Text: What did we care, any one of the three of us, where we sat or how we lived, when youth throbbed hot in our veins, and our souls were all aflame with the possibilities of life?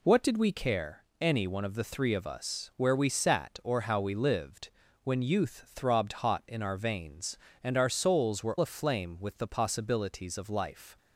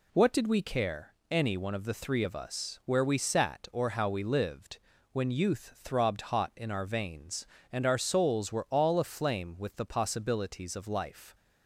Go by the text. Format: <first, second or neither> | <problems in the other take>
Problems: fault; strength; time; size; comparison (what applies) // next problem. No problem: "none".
second | skips "all"; at 8.5 s